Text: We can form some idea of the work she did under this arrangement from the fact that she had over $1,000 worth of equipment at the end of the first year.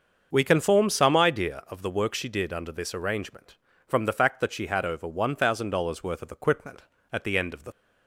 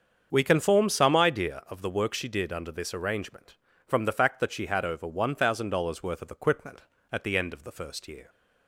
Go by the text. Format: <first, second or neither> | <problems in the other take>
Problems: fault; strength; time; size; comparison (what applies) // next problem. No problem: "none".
second | starts louder than the rest; until 1.3 s; 6.5 dB; strong in the second // stops before "first year"; at 7.7 s